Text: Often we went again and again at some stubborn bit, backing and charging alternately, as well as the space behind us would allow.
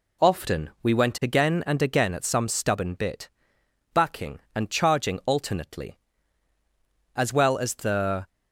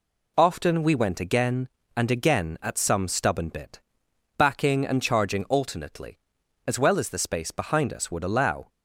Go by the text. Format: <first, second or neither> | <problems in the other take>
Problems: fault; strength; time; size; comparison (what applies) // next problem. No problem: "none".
second | stops before "space behind us would allow"; at 8.2 s